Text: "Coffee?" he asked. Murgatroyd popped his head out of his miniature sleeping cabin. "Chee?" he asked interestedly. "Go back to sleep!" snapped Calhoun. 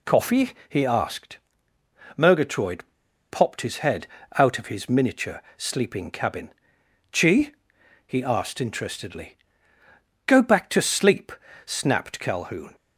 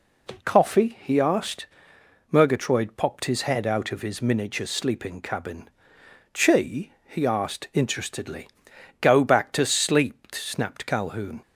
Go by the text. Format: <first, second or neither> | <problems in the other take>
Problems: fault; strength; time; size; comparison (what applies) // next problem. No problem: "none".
second | pauses between "Murgatroyd" and "popped"; noticeable; at 2.8 s; 0.47 s long // pauses between "head" and "out"; slight; at 4.0 s; 0.30 s long